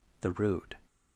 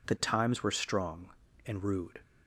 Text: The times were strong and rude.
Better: second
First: skips "times were strong and"; at 0.3 s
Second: none

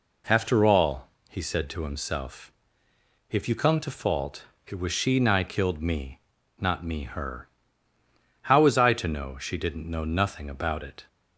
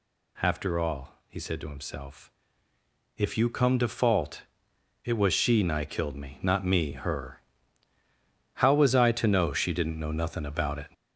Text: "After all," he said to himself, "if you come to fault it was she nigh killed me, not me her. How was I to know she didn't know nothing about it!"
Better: first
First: pauses between "fault" and "it"; slight; at 4.4 s; 0.18 s long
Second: gets louder; throughout; 6 dB // pauses between "fault" and "it"; noticeable; at 4.4 s; 0.60 s long

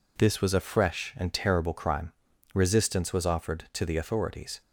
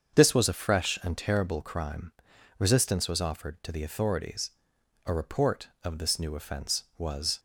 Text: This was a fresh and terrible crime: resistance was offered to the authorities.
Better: first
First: none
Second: starts louder than the rest; until 1.2 s; 7 dB // goes on to say "A report of this new offense was"; strong; from 5.0 s on; 2.3 s long

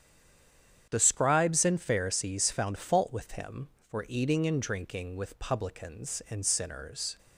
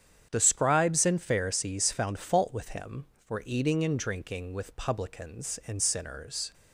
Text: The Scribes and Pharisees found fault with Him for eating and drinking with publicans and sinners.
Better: second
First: stays silent before the first word; slight; until 0.8 s; 0.8 s long // starts louder than the rest; strong; until 1.9 s; 8.5 dB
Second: starts louder than the rest; strong; until 1.3 s; 8.5 dB

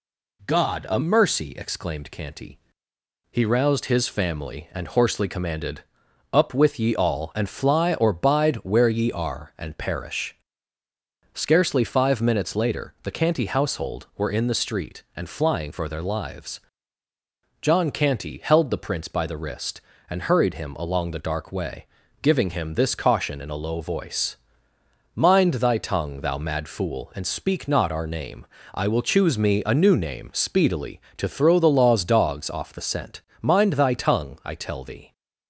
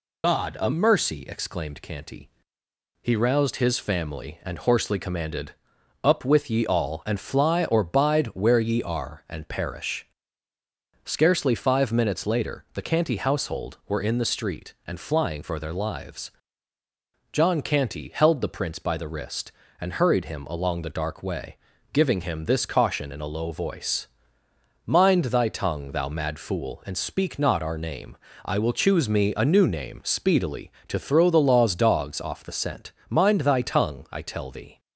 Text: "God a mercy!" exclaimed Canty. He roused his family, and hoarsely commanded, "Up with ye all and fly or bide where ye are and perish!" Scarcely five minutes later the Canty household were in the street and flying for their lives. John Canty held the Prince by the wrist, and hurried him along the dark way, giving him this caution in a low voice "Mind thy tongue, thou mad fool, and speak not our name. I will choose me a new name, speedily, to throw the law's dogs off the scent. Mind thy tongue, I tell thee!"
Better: first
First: pauses between "voice" and "Mind"; noticeable; at 24.3 s; 0.78 s long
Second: loses the start of "God"; at 0.2 s; 120 ms // pauses between "voice" and "Mind"; noticeable; at 24.0 s; 0.78 s long

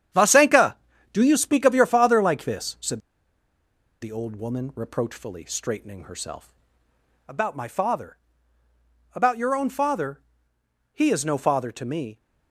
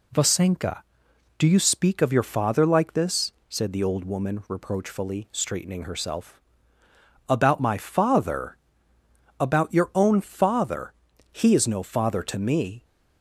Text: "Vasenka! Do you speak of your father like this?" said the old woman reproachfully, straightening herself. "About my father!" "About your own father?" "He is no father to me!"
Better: second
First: starts louder than the rest; strong; until 1.5 s; 9.5 dB // pauses between "said" and "the"; at 2.9 s; 1.0 s long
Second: none

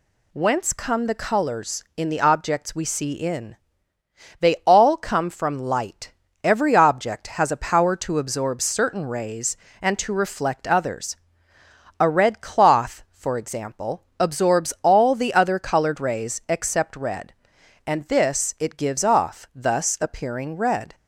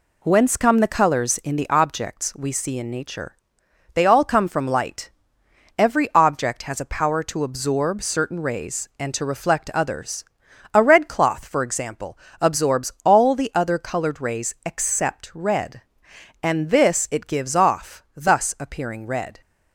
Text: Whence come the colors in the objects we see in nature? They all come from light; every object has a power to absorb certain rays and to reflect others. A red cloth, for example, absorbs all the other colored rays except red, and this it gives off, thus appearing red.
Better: second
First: skips "nature"; at 3.9 s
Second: none

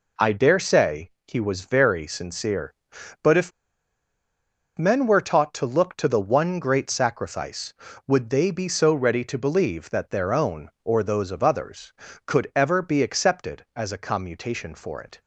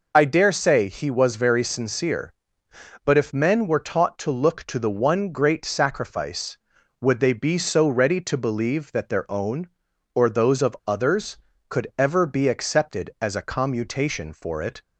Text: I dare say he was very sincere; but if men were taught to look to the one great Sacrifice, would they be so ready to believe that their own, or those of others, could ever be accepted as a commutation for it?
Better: second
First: pauses between "say" and "he"; slight; at 1.1 s; 0.16 s long // pauses between "if" and "men"; strong; at 3.5 s; 1.2 s long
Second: none

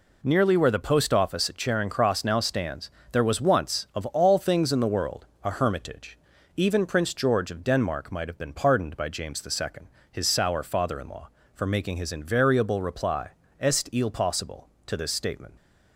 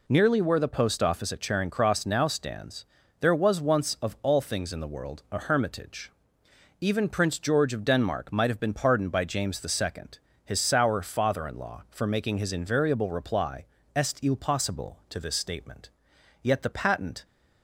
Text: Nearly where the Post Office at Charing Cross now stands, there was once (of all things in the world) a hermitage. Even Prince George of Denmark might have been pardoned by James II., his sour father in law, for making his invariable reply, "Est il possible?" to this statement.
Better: first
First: none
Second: goes on to say "Yet the patent"; noticeable; from 16.4 s on; 0.82 s long

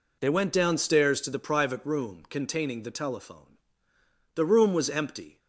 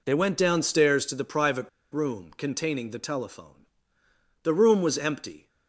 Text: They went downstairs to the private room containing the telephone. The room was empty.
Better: first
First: none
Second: pauses between "private" and "room"; slight; at 1.6 s; 0.22 s long

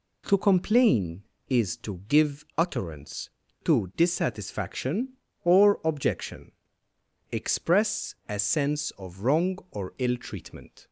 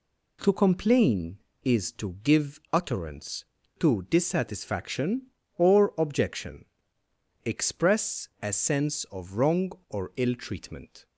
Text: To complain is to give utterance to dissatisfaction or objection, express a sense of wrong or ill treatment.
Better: neither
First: none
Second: none

